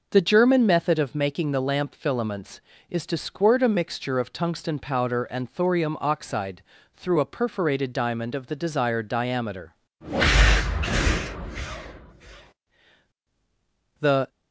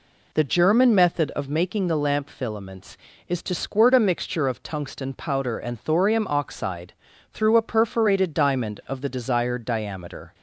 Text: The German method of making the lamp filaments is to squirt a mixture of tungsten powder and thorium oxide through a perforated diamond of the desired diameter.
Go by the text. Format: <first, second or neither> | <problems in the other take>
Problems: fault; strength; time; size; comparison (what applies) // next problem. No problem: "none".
second | pauses between "oxide" and "through"; slight; at 6.6 s; 0.34 s long; also in the second // goes on to say "The"; slight; from 13.9 s on; 0.30 s long